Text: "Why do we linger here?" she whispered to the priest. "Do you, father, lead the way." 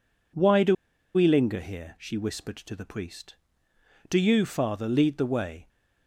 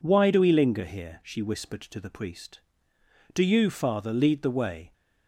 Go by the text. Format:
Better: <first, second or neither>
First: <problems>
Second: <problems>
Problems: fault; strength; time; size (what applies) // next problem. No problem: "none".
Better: second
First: pauses between "do" and "we"; at 0.7 s; 0.40 s long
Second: none